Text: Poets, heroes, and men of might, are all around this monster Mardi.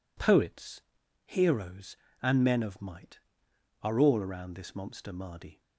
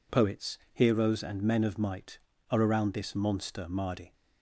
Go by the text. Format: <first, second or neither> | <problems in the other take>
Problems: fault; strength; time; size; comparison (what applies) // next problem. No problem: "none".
first | skips "all"; at 2.6 s